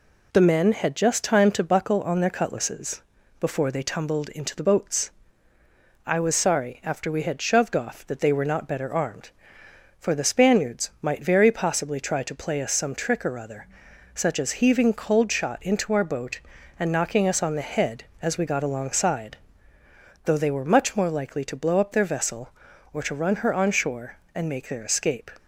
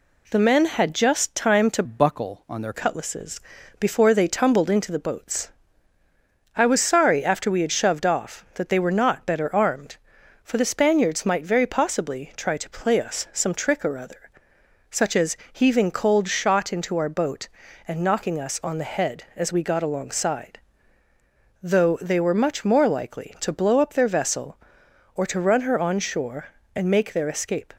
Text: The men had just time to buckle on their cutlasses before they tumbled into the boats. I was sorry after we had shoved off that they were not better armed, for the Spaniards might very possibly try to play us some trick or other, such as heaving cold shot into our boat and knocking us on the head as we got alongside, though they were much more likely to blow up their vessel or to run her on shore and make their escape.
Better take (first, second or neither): first